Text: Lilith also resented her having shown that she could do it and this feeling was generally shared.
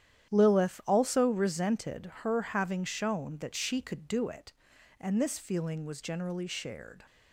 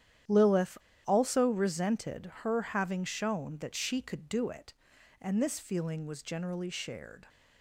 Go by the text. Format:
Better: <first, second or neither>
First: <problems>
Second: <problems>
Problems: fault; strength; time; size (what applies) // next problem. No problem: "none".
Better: first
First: starts louder than the rest; strong; until 1.3 s; 10.5 dB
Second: starts louder than the rest; strong; until 1.5 s; 10.5 dB // pauses between "Lilith" and "also"; slight; at 0.7 s; 0.30 s long